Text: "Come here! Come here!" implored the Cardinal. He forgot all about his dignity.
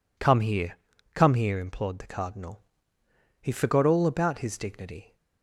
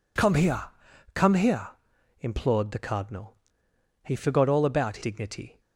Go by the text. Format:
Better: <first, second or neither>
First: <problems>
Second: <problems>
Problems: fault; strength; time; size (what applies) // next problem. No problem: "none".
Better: first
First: none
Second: skips "his"; at 5.0 s